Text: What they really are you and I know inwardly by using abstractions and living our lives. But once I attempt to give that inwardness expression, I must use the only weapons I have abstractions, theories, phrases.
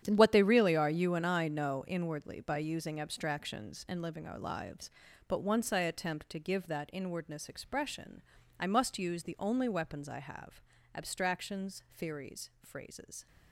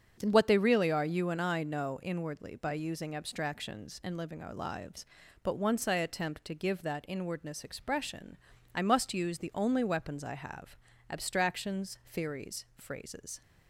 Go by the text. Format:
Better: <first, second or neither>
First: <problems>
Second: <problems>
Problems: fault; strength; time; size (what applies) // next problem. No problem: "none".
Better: second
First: gets quieter; strong; throughout; 12 dB // starts louder than the rest; strong; until 1.0 s; 9.5 dB // pauses between "have" and "abstractions"; slight; at 10.6 s; 0.34 s long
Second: starts louder than the rest; until 1.2 s; 7 dB // pauses between "have" and "abstractions"; slight; at 10.7 s; 0.34 s long